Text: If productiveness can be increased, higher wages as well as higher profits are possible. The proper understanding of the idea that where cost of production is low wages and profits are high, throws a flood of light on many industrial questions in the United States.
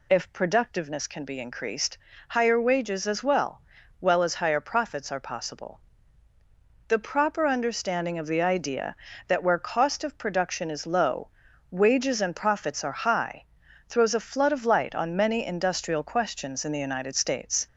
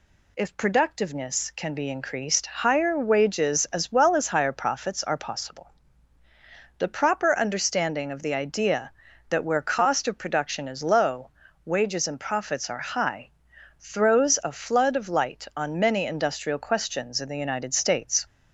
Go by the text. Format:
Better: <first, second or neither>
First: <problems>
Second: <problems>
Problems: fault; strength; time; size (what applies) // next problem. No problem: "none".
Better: second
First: says "well" twice; at 4.0 s // pauses between "low" and "wages"; at 11.2 s; 0.42 s long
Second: pauses between "low" and "wages"; slight; at 11.3 s; 0.34 s long